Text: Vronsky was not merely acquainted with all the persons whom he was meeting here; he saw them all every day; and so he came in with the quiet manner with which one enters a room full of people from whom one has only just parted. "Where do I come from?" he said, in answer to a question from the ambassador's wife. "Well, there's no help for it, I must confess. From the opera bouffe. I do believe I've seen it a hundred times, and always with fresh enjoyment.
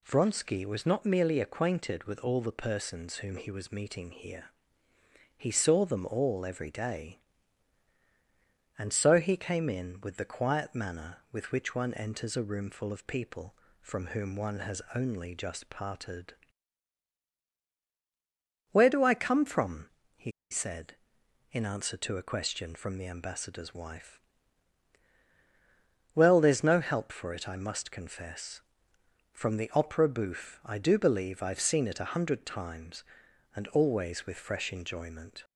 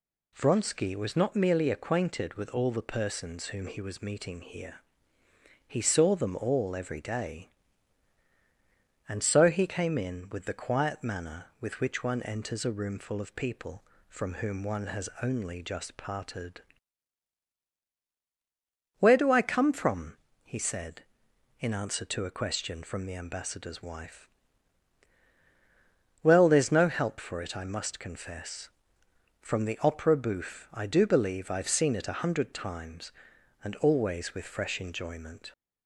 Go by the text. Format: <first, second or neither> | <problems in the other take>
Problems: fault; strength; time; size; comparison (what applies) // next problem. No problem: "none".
second | pauses between "he" and "said"; slight; at 20.3 s; 0.20 s long